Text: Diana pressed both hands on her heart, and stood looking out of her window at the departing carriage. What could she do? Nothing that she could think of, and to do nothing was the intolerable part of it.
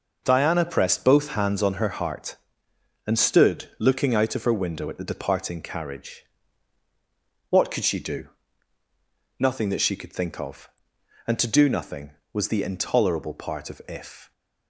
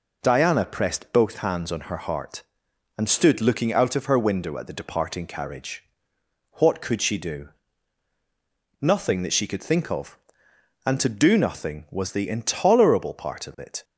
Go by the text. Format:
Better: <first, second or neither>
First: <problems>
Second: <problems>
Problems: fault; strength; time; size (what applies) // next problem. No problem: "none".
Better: second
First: says "if" for "it"; at 13.8 s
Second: none